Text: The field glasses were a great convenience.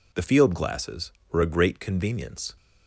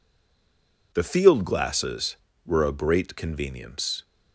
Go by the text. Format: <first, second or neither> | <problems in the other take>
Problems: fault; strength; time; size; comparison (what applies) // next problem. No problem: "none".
first | stays silent before the first word; slight; until 0.9 s; 0.9 s long